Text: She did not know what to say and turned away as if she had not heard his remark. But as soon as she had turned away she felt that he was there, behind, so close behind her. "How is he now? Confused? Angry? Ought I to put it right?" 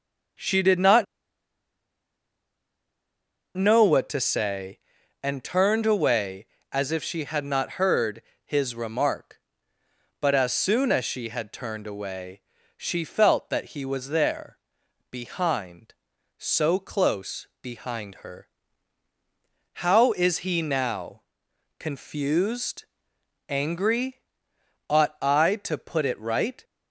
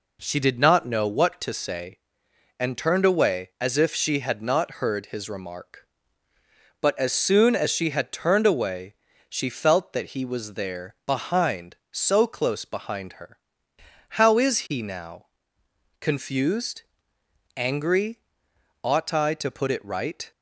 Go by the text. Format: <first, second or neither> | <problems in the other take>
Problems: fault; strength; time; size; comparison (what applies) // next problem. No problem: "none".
second | starts louder than the rest; strong; until 3.9 s; 7 dB // pauses between "not" and "know"; strong; at 1.0 s; 2.5 s long // pauses between "heard" and "his"; slight; at 8.2 s; 0.24 s long // pauses between "away" and "she"; at 12.3 s; 0.38 s long; slight in the second // pauses between "close" and "behind"; slight; at 17.4 s; 0.16 s long